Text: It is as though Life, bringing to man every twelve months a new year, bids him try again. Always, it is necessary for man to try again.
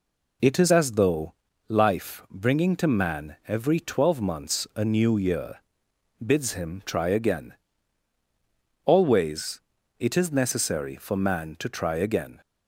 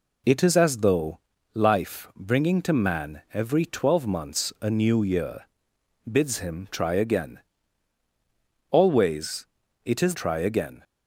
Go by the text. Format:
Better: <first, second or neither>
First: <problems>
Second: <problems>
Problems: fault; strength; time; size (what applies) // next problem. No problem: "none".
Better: first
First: pauses between "though" and "Life"; slight; at 1.3 s; 0.34 s long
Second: pauses between "though" and "Life"; slight; at 1.1 s; 0.34 s long // skips "necessary for man to"; at 10.1 s